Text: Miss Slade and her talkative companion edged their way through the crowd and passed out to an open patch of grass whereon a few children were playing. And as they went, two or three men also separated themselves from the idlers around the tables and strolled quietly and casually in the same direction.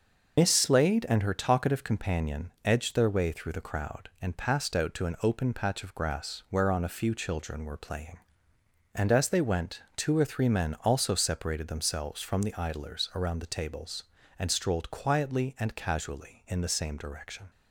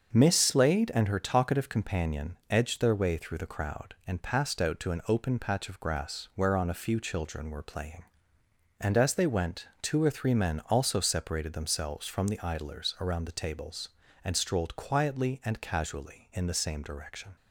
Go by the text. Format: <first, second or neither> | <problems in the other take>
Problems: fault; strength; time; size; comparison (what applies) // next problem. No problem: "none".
second | loses the start of "Miss"; at 0.3 s; 115 ms // starts louder than the rest; until 1.4 s; 6 dB; also in the second